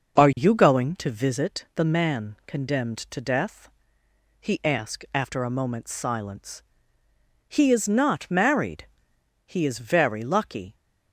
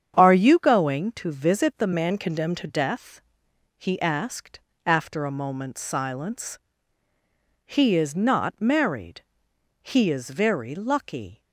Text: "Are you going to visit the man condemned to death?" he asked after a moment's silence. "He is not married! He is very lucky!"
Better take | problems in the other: first | starts louder than the rest; strong; until 1.2 s; 8 dB; noticeable in the first // changes voice from "man" to "to"; from 1.9 to 2.6 s; 0.7 s long // pauses between "asked" and "after"; slight; at 4.5 s; 0.26 s long

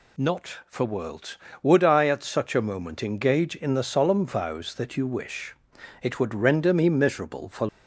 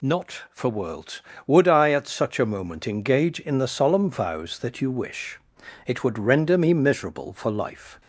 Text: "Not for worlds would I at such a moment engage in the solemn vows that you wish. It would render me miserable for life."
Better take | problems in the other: second | stops before "life"; at 7.6 s

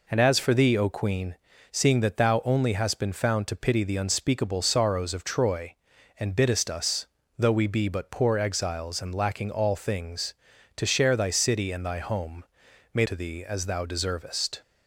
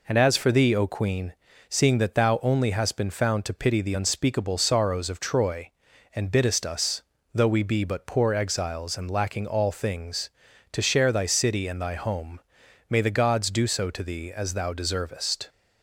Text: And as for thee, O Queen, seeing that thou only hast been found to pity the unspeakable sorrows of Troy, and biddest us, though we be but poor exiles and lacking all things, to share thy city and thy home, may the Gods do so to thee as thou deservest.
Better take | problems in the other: second | skips "the Gods do so"; at 13.0 s

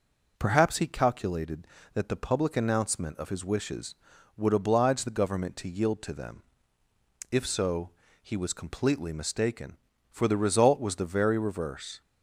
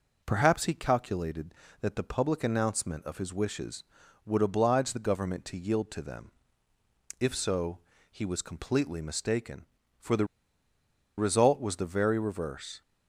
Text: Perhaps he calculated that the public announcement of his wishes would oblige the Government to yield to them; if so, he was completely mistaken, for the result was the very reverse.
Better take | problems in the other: first | pauses between "the" and "result"; noticeable; at 10.2 s; 0.93 s long

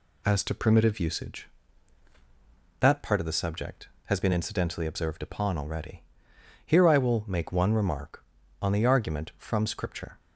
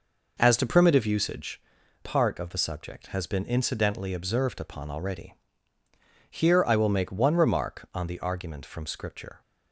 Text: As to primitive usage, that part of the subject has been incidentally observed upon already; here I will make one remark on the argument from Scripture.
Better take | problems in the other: first | skips "that"; at 1.8 s

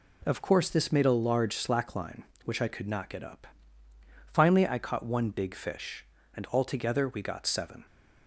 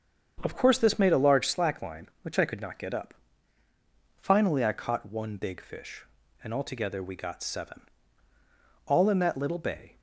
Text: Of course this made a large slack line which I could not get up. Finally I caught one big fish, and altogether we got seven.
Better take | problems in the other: first | starts louder than the rest; strong; until 1.4 s; 7.5 dB // goes on to say "All in that little bay"; noticeable; from 8.8 s on; 1.1 s long

